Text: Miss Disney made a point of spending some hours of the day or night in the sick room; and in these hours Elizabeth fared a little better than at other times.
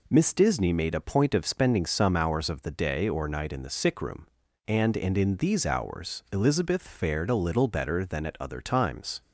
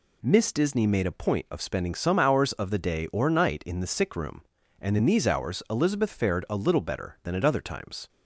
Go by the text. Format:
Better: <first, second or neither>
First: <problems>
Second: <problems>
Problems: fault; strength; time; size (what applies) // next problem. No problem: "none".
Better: second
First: says "and" twice; at 4.9 s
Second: none